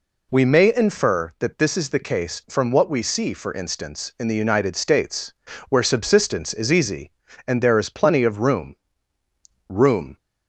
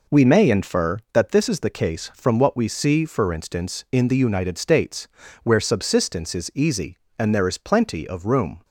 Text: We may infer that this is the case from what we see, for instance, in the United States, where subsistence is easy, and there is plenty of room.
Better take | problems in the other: second | says "room" twice; at 9.6 s

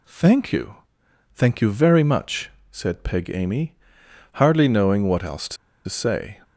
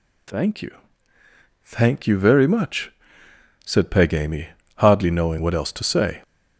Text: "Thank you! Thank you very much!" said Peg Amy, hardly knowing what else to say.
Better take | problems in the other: second | pauses between "to" and "say"; slight; at 5.5 s; 0.31 s long

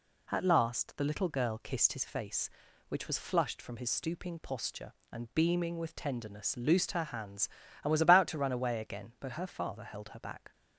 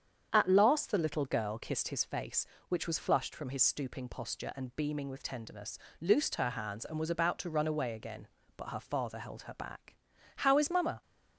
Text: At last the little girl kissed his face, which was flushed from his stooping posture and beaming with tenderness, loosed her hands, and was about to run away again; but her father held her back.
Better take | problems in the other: first | starts louder than the rest; strong; until 1.3 s; 8 dB // goes on to say "How is mamma"; noticeable; from 10.3 s on; 0.66 s long

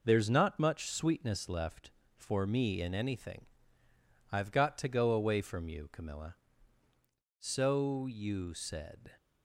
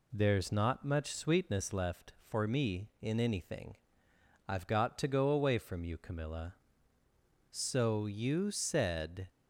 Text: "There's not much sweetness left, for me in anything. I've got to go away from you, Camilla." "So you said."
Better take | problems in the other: neither | none

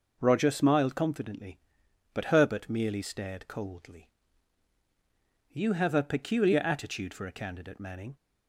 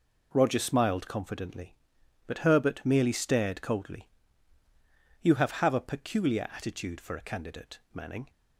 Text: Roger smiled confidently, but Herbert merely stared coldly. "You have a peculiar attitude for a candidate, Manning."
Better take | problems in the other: first | says "have" twice; at 5.5 s

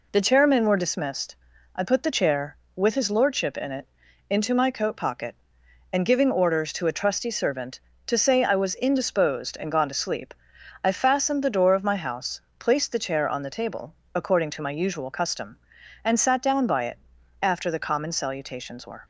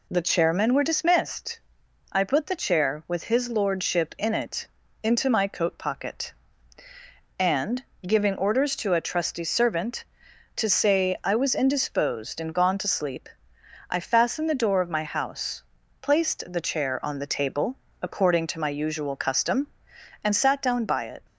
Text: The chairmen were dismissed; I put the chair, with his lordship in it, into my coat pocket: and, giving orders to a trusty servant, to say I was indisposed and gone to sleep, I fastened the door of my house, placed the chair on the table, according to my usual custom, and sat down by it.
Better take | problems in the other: second | goes on to say "After the common salutations were"; from 17.4 s on; 1.6 s long

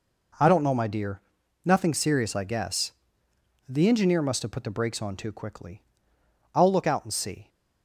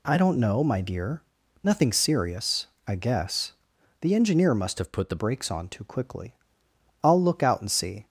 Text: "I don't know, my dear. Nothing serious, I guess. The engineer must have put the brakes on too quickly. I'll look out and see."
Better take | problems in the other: first | changes voice from "have" to "the"; from 4.7 to 5.1 s; 0.4 s long

